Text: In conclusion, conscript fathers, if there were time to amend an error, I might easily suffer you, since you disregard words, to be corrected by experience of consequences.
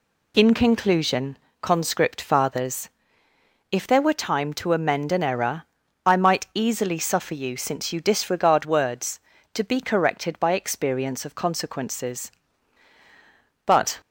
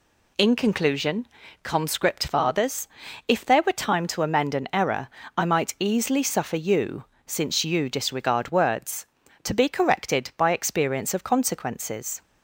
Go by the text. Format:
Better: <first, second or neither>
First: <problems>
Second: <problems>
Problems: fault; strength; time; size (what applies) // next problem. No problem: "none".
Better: second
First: goes on to say "But"; slight; from 13.6 s on; 0.32 s long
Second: none